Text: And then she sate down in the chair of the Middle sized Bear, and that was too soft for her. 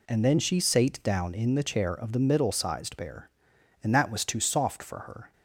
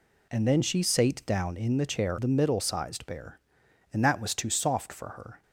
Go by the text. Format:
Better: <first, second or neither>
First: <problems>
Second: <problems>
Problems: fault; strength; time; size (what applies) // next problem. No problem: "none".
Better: first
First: none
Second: skips "of"; at 2.1 s